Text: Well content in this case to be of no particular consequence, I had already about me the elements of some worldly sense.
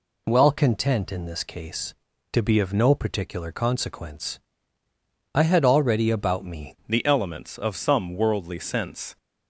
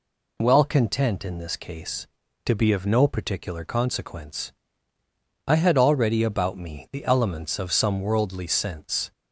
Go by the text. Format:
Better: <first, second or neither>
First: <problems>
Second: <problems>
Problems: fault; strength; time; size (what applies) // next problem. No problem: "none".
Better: second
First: changes voice at "the"; from 6.8 s on; 2.3 s long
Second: none